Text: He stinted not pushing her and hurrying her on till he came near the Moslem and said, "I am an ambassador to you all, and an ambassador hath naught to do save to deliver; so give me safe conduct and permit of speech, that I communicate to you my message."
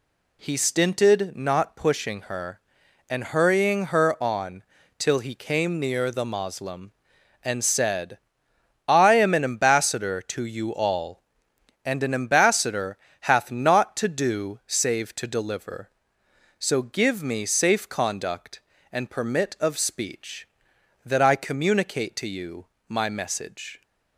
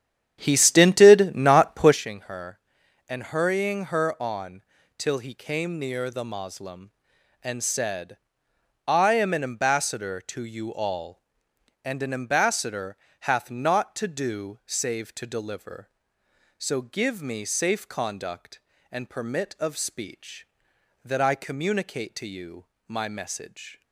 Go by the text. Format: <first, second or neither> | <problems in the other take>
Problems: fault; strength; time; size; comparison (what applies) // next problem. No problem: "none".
first | starts louder than the rest; strong; until 2.0 s; 9.5 dB // pauses between "on" and "till"; slight; at 4.6 s; 0.36 s long; slight in the first // pauses between "ambassador" and "hath"; slight; at 12.9 s; 0.26 s long; slight in the first // pauses between "you" and "my"; slight; at 22.6 s; 0.24 s long; slight in the first